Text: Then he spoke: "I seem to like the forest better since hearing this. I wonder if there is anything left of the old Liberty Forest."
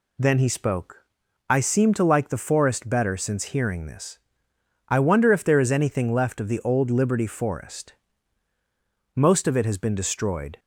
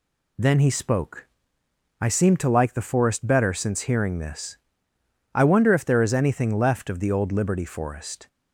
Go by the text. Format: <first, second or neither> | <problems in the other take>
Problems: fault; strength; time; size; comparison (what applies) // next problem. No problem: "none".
second | goes on to say "Most of it has been destroyed"; from 9.1 s on; 1.4 s long